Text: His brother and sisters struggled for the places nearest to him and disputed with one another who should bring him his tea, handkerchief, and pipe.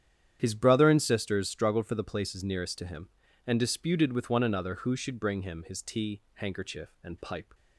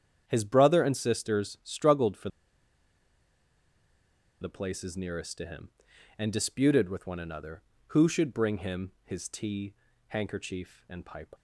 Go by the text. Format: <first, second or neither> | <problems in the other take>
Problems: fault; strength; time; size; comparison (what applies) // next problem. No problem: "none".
first | starts louder than the rest; strong; until 1.2 s; 8.5 dB; strong in the first // pauses between "for" and "the"; strong; at 2.2 s; 2.1 s long